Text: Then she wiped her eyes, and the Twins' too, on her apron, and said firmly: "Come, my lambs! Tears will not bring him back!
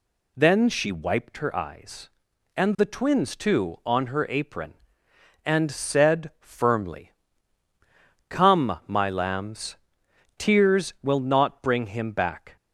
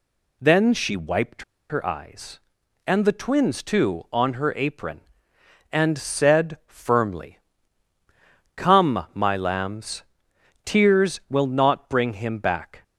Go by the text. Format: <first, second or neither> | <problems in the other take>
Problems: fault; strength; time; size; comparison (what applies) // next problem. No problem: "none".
first | pauses between "wiped" and "her"; slight; at 1.4 s; 0.26 s long